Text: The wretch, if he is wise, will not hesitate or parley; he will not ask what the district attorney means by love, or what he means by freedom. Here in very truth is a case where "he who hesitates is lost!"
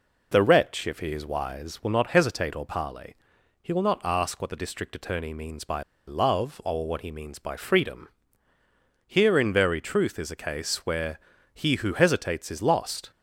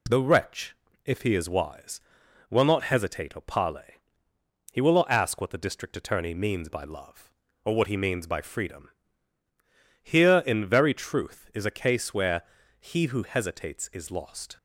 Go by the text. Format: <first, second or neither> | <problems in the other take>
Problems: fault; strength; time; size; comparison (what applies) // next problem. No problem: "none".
second | pauses between "by" and "love"; slight; at 5.8 s; 0.24 s long // pauses between "where" and "he"; slight; at 11.1 s; 0.34 s long; also in the second